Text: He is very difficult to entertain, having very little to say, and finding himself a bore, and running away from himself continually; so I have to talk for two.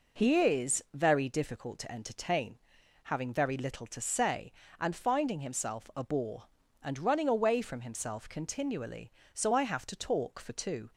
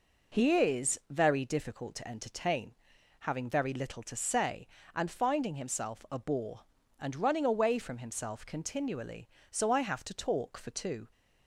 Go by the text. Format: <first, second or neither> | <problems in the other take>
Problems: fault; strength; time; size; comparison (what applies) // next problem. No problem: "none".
neither | none